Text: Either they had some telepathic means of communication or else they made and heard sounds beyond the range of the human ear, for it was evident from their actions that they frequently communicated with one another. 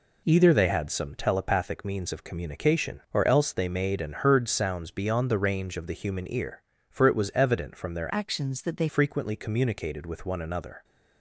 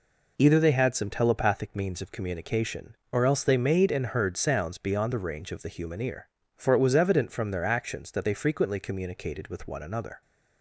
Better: second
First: changes voice from "actions" to "they"; from 8.1 to 8.8 s; 0.7 s long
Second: none

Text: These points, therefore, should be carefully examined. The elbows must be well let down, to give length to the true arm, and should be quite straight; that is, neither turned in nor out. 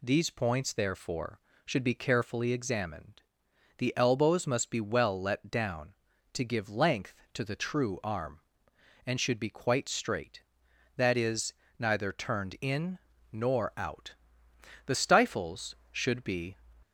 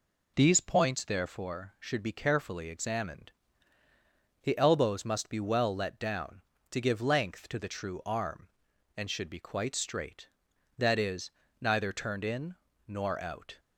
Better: second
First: pauses between "in" and "nor"; slight; at 12.9 s; 0.32 s long // goes on to say "The stifles should be"; strong; from 14.8 s on; 1.7 s long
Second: pauses between "in" and "nor"; slight; at 12.5 s; 0.30 s long

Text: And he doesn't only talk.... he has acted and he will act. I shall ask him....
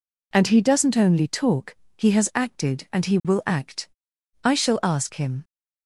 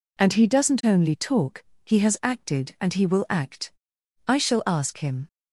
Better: neither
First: none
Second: none

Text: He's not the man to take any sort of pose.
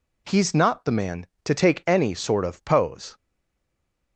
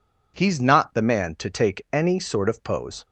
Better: second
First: stays silent after the last word; from 3.1 s on; 1.0 s long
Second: none

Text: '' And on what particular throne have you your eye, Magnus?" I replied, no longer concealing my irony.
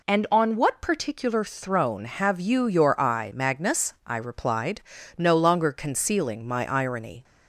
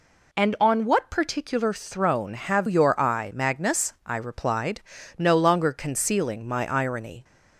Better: first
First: none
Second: skips "you"; at 2.6 s

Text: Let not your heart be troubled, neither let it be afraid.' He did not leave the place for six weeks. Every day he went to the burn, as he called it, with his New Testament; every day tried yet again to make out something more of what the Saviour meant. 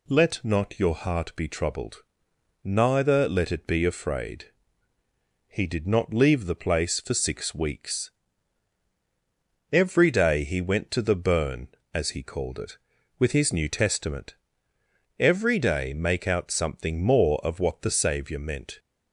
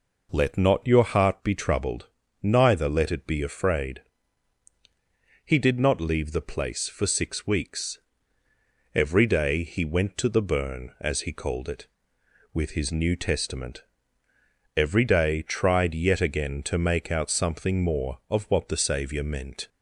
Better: second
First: skips "tried yet again to"; at 15.9 s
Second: none

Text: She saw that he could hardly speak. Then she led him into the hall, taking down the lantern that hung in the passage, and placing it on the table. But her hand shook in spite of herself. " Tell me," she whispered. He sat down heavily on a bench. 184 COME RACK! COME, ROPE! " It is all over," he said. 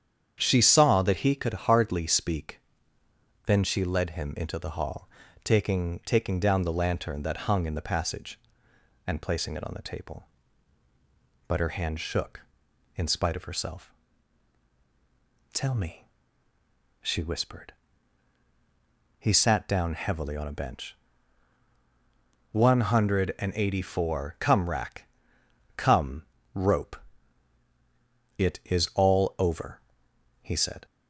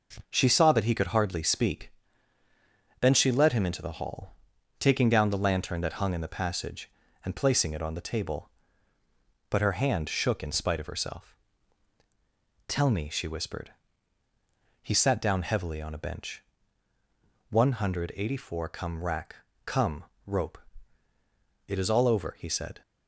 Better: second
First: starts louder than the rest; strong; until 1.4 s; 8.5 dB // says "taking" twice; at 6.0 s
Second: none

